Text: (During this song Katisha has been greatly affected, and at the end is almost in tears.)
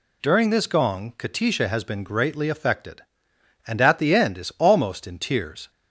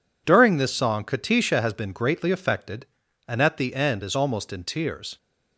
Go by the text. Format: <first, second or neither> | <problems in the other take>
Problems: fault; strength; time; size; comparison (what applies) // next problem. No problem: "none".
second | says "gong" for "song"; at 0.6 s